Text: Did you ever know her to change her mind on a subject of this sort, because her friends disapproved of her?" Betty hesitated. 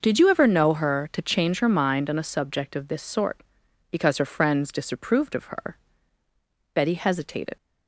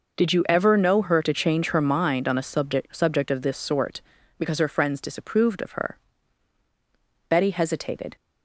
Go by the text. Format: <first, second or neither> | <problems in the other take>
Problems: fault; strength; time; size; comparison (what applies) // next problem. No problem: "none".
first | says "subject" twice; at 2.9 s